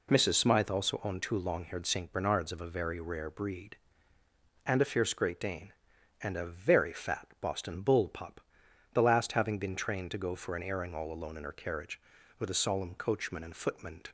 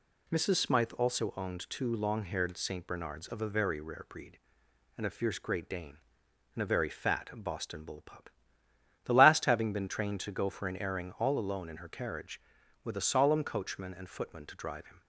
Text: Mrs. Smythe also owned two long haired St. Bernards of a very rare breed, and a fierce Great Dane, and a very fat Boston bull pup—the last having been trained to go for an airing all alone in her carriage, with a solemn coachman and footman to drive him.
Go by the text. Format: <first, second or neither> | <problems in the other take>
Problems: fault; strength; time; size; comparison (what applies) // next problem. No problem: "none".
second | stops before "drive him"; at 14.0 s